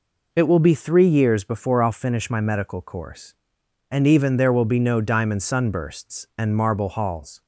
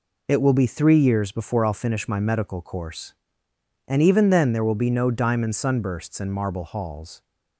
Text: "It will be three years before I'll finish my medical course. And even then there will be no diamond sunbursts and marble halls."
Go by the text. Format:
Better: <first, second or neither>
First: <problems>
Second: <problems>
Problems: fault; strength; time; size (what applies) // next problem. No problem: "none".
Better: second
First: skips "then"; at 4.3 s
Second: none